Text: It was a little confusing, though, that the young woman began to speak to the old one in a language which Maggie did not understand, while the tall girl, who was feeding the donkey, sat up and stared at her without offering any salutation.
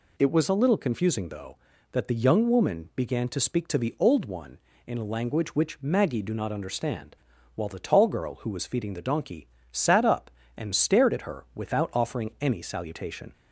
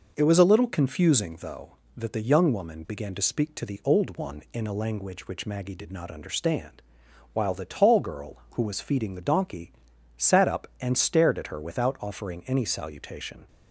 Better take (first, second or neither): second